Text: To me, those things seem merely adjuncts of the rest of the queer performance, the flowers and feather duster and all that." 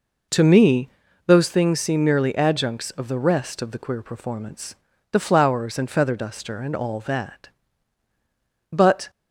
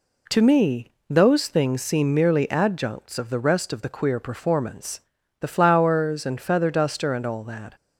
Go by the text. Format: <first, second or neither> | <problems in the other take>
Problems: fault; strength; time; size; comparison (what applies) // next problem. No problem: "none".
second | goes on to say "But"; slight; from 8.7 s on; 0.38 s long